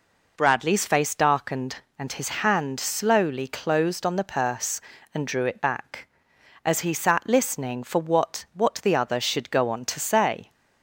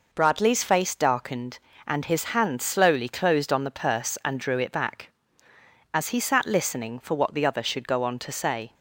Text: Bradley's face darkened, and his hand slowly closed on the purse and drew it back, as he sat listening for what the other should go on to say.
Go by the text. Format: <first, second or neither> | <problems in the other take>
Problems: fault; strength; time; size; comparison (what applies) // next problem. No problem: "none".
second | says "what" twice; at 8.5 s